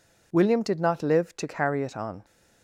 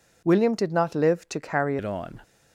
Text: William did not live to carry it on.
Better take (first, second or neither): first